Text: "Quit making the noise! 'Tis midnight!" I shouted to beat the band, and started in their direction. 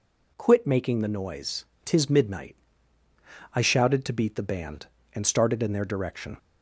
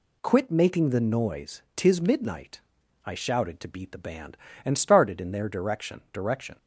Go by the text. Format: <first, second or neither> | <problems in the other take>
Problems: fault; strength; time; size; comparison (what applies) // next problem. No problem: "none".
first | says "direction" twice; at 6.1 s